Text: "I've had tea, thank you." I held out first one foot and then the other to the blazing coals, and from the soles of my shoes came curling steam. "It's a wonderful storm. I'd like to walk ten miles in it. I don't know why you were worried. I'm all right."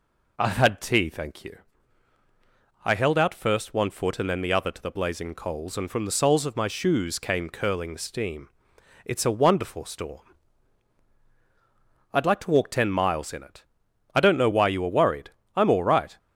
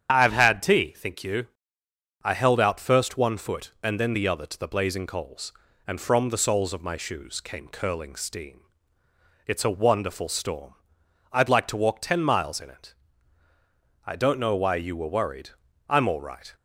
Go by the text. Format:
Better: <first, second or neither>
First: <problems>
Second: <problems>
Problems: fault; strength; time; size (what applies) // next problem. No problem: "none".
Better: first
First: none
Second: starts louder than the rest; strong; until 1.1 s; 8.5 dB // says "think" for "thank"; at 0.9 s